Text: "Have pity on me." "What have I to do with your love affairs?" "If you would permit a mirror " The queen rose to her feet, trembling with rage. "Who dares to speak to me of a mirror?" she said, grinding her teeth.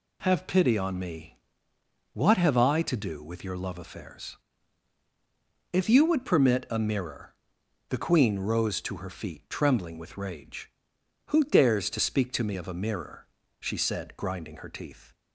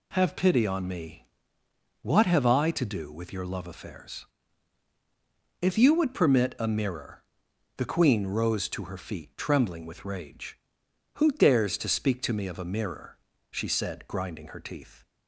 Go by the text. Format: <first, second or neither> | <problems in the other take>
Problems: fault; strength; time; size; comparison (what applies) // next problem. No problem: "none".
neither | none